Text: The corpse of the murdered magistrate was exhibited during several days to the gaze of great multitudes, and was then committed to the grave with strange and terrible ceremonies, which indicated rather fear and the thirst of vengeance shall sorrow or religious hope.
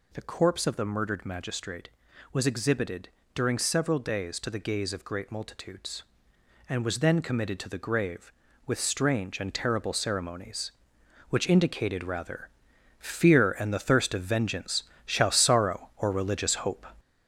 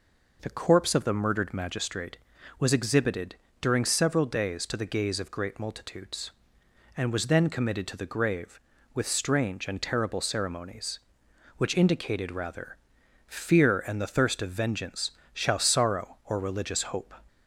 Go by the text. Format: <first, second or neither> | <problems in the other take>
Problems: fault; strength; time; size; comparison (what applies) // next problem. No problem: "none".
second | gets louder; noticeable; throughout; 6 dB // pauses between "exhibited" and "during"; slight; at 3.0 s; 0.24 s long; slight in the second // pauses between "rather" and "fear"; noticeable; at 12.4 s; 0.50 s long; noticeable in the second // pauses between "vengeance" and "shall"; slight; at 14.8 s; 0.22 s long; slight in the second